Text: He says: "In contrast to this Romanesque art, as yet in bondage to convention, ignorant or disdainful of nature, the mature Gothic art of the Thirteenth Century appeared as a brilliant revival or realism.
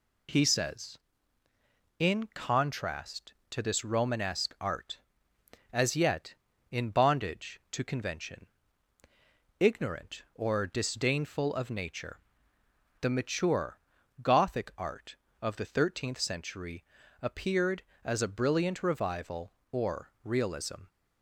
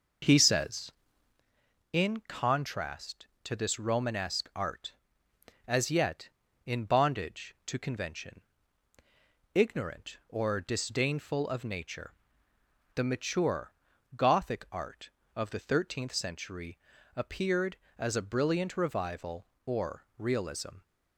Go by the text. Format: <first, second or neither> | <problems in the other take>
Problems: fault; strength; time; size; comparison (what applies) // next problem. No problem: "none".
first | starts louder than the rest; noticeable; until 1.6 s; 5.5 dB // pauses between "mature" and "Gothic"; at 13.7 s; 0.42 s long; also in the first // pauses between "Century" and "appeared"; at 16.7 s; 0.38 s long; also in the first